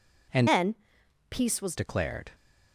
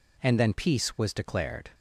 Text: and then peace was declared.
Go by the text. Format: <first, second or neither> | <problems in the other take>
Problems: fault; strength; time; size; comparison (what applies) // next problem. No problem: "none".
second | changes voice from "then" to "was"; from 0.4 to 1.7 s; 1.3 s long // pauses between "then" and "peace"; noticeable; at 0.7 s; 0.54 s long